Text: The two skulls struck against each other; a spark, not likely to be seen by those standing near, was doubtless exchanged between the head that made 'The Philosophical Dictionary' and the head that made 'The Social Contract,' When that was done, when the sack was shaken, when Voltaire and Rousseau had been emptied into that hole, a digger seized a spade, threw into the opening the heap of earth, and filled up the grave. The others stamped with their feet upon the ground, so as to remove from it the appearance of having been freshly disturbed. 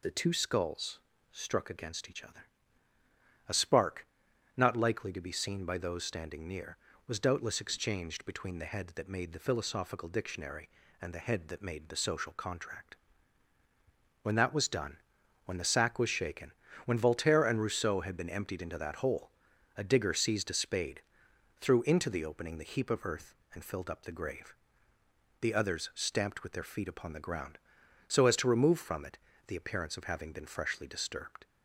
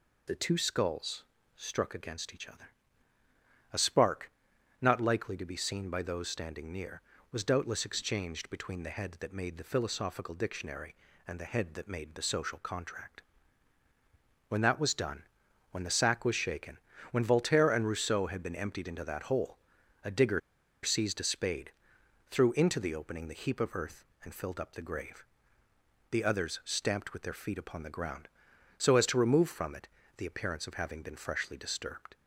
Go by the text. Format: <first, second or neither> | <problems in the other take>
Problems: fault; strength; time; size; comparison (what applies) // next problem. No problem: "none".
first | pauses between "skulls" and "struck"; slight; at 1.2 s; 0.34 s long; slight in the first // pauses between "digger" and "seized"; at 20.4 s; 0.43 s long // pauses between "it" and "the"; slight; at 29.8 s; 0.28 s long; slight in the first